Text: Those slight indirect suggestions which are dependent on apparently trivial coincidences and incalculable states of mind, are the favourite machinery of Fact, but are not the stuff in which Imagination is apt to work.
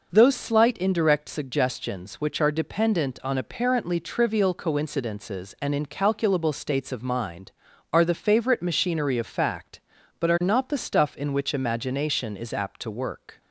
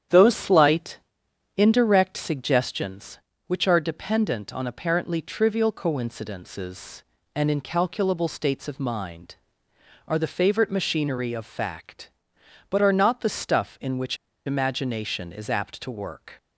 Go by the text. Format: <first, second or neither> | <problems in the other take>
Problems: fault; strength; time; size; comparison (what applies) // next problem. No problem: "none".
first | starts louder than the rest; strong; until 1.6 s; 9.5 dB // pauses between "slight" and "indirect"; noticeable; at 0.9 s; 0.58 s long // pauses between "which" and "Imagination"; slight; at 14.1 s; 0.29 s long